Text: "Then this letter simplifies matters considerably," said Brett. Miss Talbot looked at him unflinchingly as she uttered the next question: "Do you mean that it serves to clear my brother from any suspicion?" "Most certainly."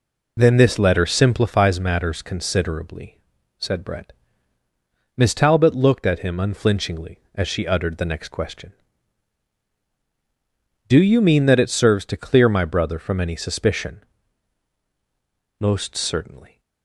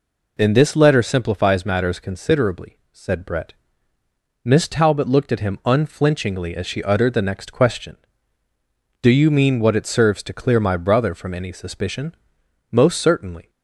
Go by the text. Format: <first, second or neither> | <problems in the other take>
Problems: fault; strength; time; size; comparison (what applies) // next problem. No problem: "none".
first | says "what" for "that"; at 9.5 s